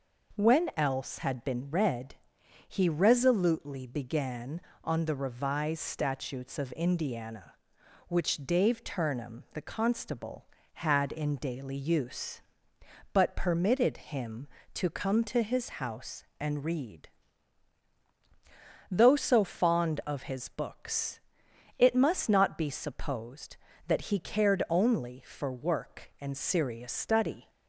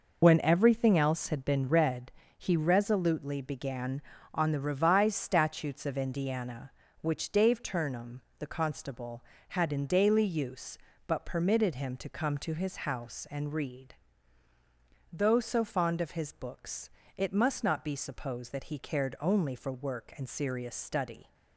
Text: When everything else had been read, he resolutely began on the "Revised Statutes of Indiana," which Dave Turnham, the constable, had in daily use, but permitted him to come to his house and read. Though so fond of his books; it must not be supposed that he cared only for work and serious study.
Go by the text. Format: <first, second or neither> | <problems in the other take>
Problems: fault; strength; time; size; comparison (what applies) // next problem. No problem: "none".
second | skips "everything"; at 0.7 s